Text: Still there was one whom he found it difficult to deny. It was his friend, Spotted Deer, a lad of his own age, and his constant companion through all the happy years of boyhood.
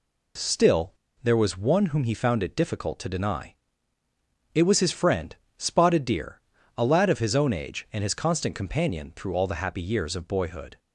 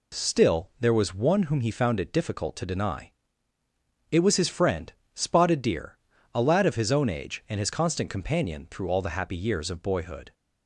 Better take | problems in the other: second | pauses between "Still" and "there"; slight; at 0.9 s; 0.29 s long

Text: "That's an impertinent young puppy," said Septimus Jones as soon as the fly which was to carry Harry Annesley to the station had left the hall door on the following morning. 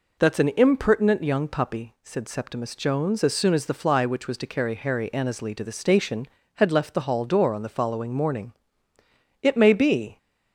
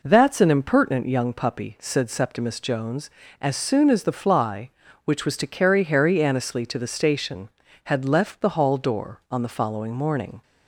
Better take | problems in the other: second | goes on to say "It may be"; noticeable; from 9.4 s on; 0.74 s long

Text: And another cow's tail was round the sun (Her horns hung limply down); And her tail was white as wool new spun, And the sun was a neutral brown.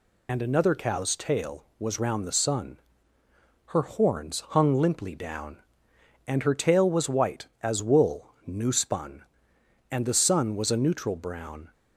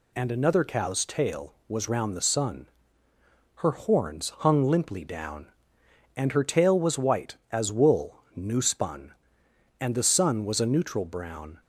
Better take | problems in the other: second | loses the start of "And"; at 0.2 s; 35 ms // pauses between "wool" and "new"; slight; at 8.2 s; 0.16 s long; slight in the second

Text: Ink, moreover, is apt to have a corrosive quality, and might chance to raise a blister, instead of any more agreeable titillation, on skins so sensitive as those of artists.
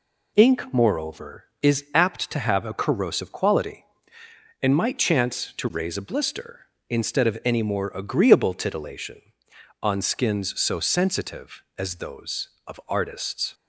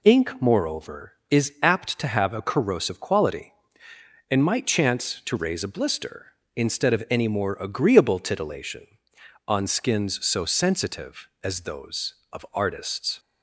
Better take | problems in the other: neither | none

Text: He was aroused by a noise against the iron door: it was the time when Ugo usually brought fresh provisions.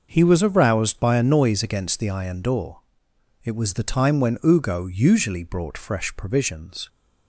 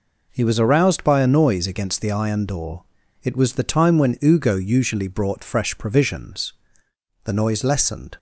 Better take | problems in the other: first | goes on to say "The noise lessened"; noticeable; from 7.2 s on; 0.90 s long

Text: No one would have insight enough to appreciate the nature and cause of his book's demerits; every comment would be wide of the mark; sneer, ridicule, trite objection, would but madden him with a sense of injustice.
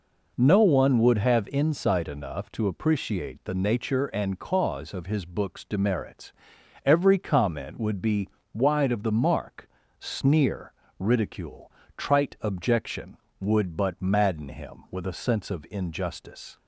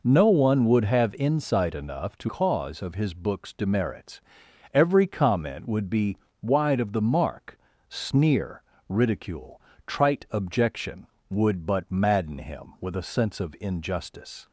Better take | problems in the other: first | skips "appreciate the nature and"; at 2.2 s // pauses between "be" and "wide"; slight; at 6.1 s; 0.24 s long; slight in the first

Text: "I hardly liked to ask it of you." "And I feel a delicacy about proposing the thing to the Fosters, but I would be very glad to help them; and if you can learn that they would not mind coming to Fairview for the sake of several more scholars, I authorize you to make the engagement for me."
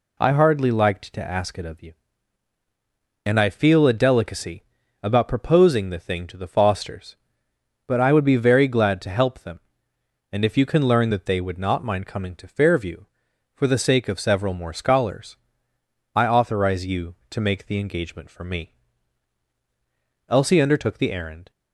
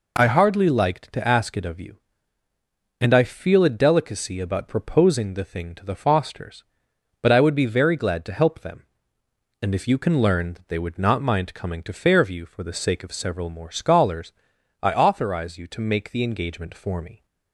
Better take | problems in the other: second | pauses between "delicacy" and "about"; at 4.6 s; 0.38 s long // goes on to say "Elsie undertook the errand"; noticeable; from 20.2 s on; 1.2 s long

